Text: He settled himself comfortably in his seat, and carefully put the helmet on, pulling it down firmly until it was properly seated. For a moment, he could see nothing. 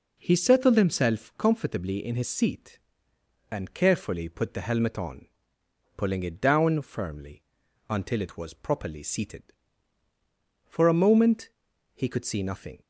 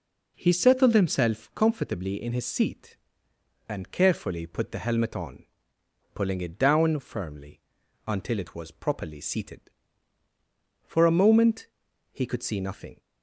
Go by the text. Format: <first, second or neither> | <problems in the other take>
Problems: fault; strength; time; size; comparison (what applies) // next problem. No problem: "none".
neither | pauses between "firmly" and "until"; noticeable; the same in both